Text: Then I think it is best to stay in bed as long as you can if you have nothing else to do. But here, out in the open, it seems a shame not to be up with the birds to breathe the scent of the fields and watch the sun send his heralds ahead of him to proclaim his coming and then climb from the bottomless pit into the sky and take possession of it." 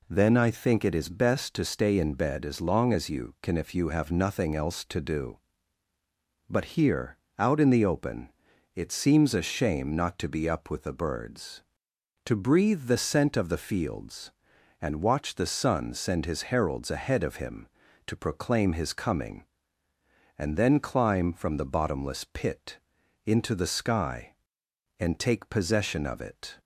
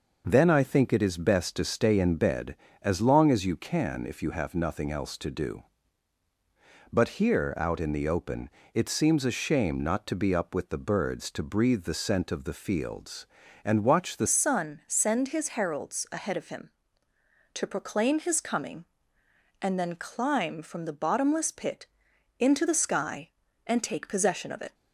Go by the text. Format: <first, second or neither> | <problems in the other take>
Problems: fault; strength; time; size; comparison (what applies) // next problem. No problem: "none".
first | changes voice at "sun"; from 14.2 s on; 10.5 s long // pauses between "pit" and "into"; noticeable; at 21.8 s; 0.54 s long; noticeable in the first